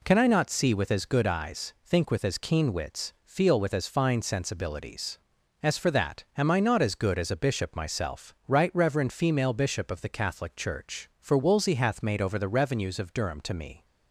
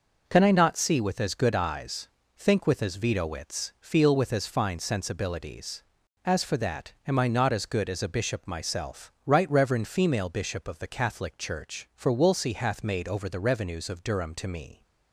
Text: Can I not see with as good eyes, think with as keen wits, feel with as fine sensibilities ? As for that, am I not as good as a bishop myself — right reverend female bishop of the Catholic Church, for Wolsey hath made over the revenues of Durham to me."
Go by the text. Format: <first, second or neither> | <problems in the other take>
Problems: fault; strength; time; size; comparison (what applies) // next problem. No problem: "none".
first | says "veto" for "keen"; at 2.9 s